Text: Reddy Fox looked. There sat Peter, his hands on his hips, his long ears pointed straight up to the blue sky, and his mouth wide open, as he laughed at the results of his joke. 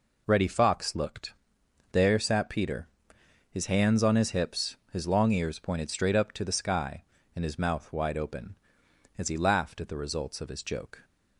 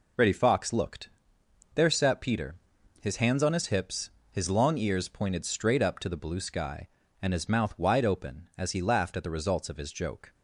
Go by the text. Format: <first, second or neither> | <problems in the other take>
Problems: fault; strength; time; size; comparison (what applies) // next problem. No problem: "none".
second | skips "blue"; at 6.5 s